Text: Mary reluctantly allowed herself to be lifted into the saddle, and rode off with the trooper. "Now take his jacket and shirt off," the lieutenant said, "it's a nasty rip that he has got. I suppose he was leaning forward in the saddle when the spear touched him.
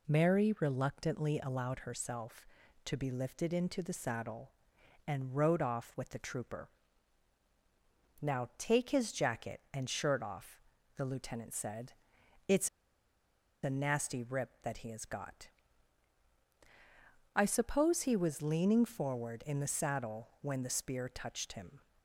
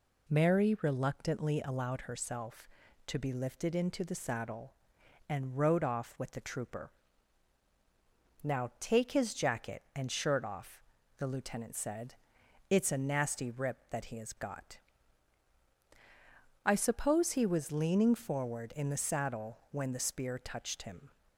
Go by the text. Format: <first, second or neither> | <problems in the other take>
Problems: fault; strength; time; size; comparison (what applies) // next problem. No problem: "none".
second | pauses between "it's" and "a"; noticeable; at 12.6 s; 0.95 s long